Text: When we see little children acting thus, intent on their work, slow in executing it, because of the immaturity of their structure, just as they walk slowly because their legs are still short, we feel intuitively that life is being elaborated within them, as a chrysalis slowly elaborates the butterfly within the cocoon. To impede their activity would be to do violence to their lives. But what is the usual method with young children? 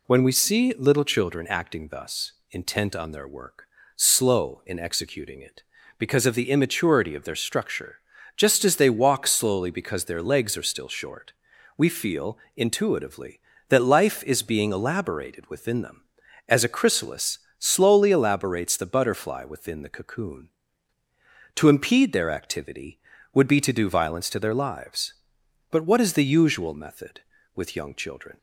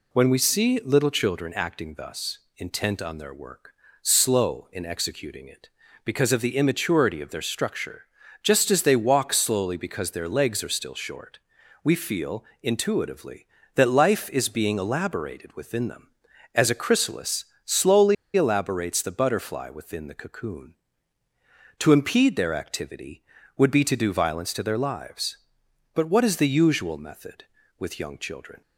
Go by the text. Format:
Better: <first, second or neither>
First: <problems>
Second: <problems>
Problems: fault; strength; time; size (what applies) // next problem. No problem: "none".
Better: first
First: pauses between "feel" and "intuitively"; slight; at 12.3 s; 0.18 s long // pauses between "chrysalis" and "slowly"; slight; at 17.3 s; 0.18 s long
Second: pauses between "feel" and "intuitively"; slight; at 12.4 s; 0.18 s long // pauses between "chrysalis" and "slowly"; slight; at 17.4 s; 0.18 s long // pauses between "slowly" and "elaborates"; slight; at 18.1 s; 0.21 s long